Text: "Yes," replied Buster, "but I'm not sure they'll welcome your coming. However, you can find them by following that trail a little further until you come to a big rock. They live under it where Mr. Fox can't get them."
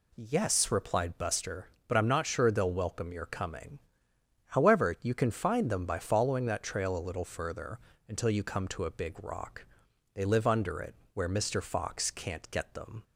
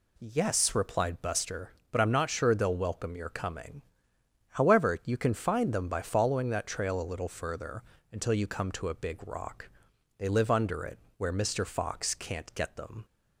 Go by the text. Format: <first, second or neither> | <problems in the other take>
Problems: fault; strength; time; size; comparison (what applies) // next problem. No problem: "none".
neither | pauses between "further" and "until"; slight; the same in both // pauses between "it" and "where"; slight; the same in both